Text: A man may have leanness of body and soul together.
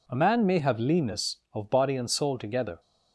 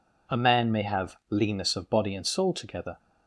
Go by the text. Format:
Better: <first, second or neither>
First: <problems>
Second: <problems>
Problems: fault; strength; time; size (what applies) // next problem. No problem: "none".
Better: neither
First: none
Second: none